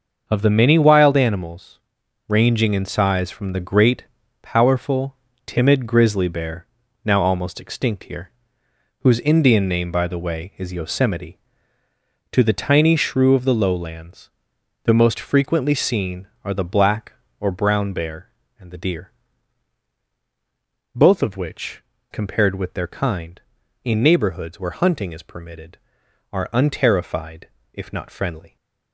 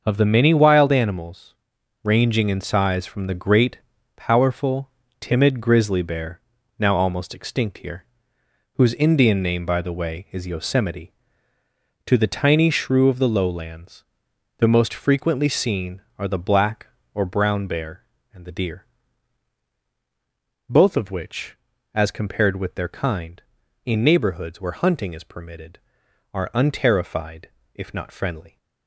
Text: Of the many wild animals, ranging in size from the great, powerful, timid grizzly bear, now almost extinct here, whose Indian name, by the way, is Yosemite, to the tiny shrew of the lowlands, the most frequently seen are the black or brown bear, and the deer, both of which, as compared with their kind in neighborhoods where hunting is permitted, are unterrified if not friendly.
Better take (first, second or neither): second